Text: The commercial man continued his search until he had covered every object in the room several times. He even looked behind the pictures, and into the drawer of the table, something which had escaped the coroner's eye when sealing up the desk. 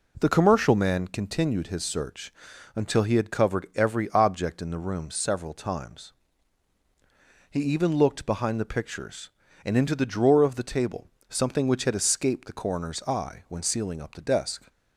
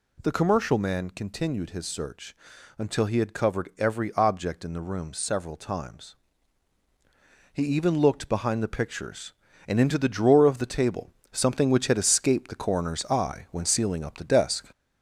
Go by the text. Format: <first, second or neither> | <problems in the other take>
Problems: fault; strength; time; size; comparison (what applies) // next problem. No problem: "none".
first | gets louder; slight; throughout; 3.5 dB // pauses between "search" and "until"; at 2.3 s; 0.42 s long; also in the first